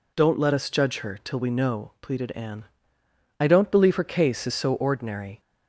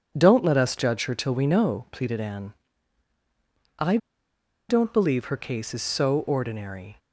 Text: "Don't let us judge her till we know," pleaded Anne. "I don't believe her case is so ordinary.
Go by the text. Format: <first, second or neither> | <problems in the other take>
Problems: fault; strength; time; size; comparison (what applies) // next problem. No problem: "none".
first | pauses between "I" and "don't"; noticeable; at 3.9 s; 0.72 s long